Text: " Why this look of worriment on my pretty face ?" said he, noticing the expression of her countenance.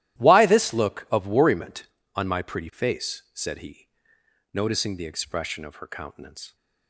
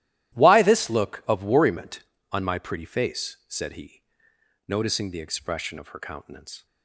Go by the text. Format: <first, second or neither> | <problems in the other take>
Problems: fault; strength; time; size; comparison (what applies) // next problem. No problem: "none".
neither | starts louder than the rest; strong; the same in both